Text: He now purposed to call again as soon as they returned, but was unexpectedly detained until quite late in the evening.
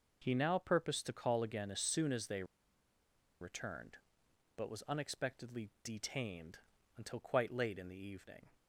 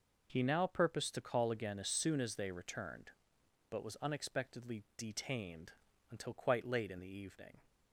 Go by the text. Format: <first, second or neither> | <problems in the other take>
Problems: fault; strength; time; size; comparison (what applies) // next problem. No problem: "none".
second | pauses between "they" and "returned"; noticeable; at 2.4 s; 0.96 s long // pauses between "detained" and "until"; slight; at 6.5 s; 0.36 s long; slight in the second